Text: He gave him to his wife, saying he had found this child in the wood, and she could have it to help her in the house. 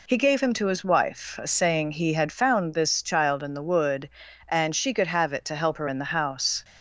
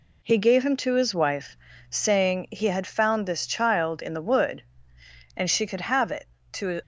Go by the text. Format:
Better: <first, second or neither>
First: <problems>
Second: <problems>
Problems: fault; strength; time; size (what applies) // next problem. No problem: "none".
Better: first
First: none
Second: stops before "help her in the house"; at 6.8 s